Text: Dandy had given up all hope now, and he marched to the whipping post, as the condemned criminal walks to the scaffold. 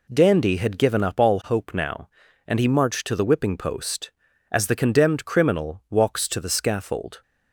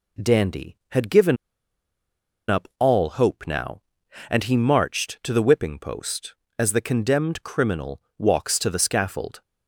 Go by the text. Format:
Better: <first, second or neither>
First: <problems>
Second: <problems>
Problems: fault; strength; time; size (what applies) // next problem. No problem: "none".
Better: first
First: none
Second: pauses between "given" and "up"; at 1.3 s; 1.1 s long // pauses between "criminal" and "walks"; slight; at 8.0 s; 0.16 s long